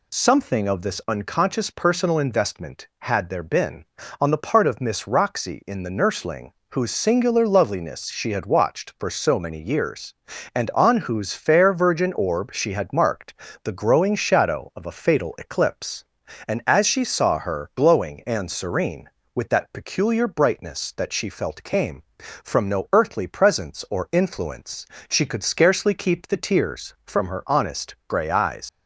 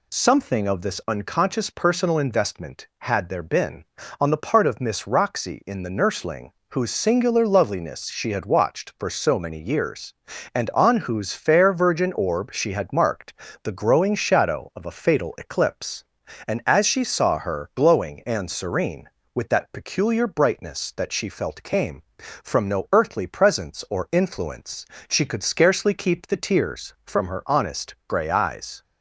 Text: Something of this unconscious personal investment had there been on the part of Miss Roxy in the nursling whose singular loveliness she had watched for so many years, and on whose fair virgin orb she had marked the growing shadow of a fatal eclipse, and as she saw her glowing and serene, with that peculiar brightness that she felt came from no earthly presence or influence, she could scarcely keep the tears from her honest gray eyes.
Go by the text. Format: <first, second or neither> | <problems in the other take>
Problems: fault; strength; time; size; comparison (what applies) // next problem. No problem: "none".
second | pauses between "nursling" and "whose"; slight; at 6.5 s; 0.20 s long; slight in the second // pauses between "marked" and "the"; slight; at 13.3 s; 0.28 s long; slight in the second // leaves "eyes" unfinished; at 28.6 s; 135 ms